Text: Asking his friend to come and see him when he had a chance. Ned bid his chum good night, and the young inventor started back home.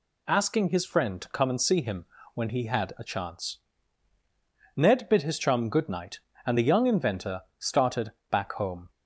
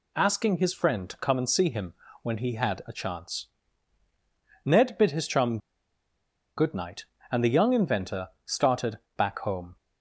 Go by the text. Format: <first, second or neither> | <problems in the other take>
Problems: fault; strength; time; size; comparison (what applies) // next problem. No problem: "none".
first | pauses between "him" and "when"; slight; at 1.9 s; 0.28 s long; slight in the first // pauses between "chum" and "good"; at 5.5 s; 0.99 s long // pauses between "inventor" and "started"; slight; at 8.2 s; 0.16 s long; slight in the first // pauses between "started" and "back"; slight; at 8.9 s; 0.18 s long; slight in the first